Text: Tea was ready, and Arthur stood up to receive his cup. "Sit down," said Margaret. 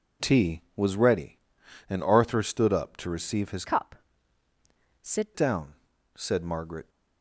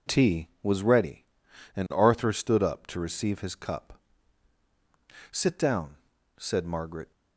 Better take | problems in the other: second | changes voice from "cup" to "Sit"; from 3.6 to 5.3 s; 1.7 s long

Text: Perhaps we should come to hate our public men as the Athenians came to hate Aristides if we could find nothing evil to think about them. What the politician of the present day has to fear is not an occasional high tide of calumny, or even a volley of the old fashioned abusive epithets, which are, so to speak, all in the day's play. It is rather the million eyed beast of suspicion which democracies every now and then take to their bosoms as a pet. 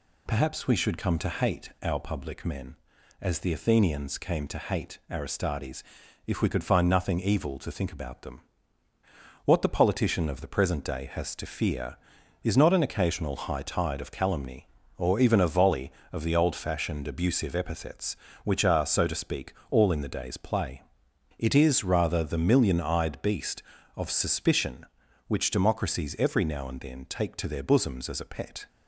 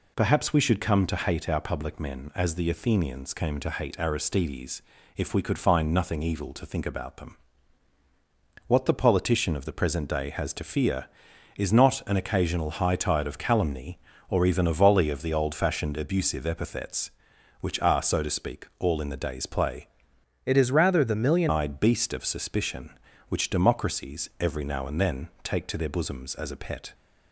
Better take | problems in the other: first | pauses between "Aristides" and "if"; slight; at 4.7 s; 0.36 s long; also in the first // changes voice from "It" to "million"; from 20.4 to 21.5 s; 1.1 s long

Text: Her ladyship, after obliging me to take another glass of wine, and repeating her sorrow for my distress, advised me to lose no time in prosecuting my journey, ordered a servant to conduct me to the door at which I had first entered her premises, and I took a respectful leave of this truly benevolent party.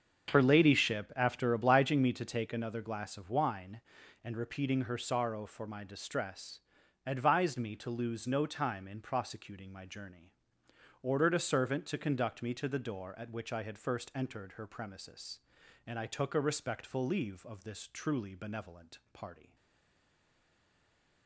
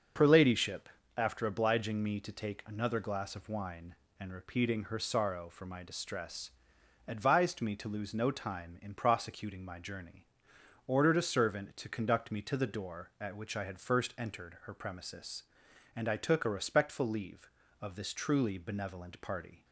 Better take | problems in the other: second | starts louder than the rest; until 1.3 s; 7 dB; also in the second // stays silent after the last word; noticeable; from 19.5 s on; 1.7 s long

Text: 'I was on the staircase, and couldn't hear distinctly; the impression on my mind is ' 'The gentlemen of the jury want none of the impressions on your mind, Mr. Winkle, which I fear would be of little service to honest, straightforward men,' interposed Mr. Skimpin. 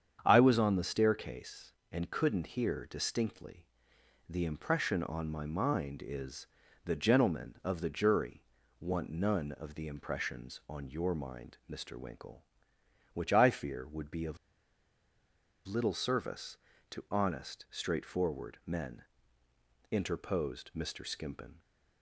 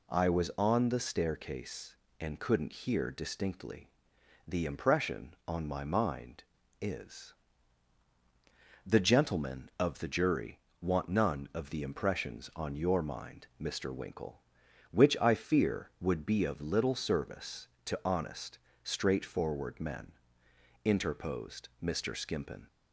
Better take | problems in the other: second | starts louder than the rest; strong; until 1.2 s; 8 dB // pauses between "jury" and "want"; slight; at 8.4 s; 0.36 s long; slight in the second // pauses between "of" and "little"; strong; at 14.3 s; 1.3 s long

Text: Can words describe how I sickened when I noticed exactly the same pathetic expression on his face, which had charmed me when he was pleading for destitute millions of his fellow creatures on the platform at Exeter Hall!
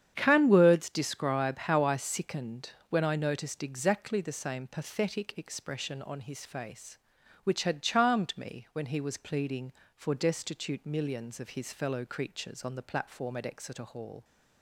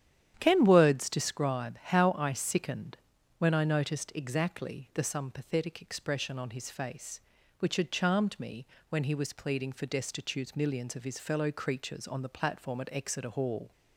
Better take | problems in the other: first | starts louder than the rest; strong; until 1.4 s; 10 dB; strong in the first // pauses between "sickened" and "when"; at 2.9 s; 0.42 s long; slight in the first // says "some" for "same"; at 5.0 s // pauses between "me" and "when"; slight; at 8.6 s; 0.22 s long

